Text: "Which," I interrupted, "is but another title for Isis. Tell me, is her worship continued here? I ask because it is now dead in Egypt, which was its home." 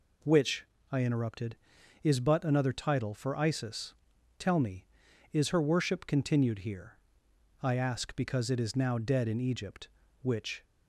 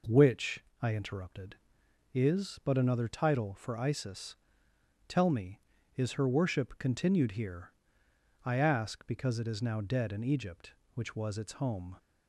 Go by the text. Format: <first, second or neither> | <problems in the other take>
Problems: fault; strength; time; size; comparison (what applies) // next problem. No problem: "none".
second | stops before "was its home"; at 10.6 s